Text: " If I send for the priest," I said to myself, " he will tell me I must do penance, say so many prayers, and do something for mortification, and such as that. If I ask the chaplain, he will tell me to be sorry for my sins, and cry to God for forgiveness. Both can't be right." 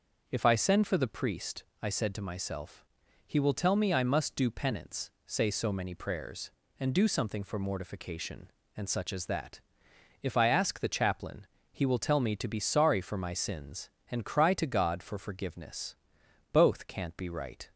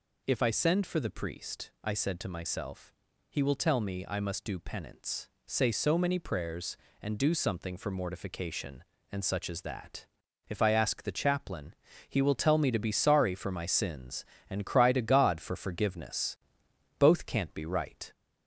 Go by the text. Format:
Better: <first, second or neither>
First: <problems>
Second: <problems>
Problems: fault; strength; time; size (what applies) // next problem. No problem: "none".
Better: first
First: none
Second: gets louder; slight; throughout; 3 dB